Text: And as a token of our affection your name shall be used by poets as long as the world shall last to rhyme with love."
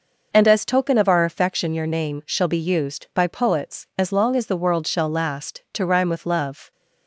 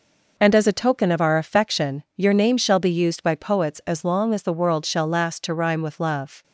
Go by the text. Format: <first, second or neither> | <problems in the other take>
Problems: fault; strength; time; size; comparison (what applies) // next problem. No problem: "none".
second | skips "a"; at 0.6 s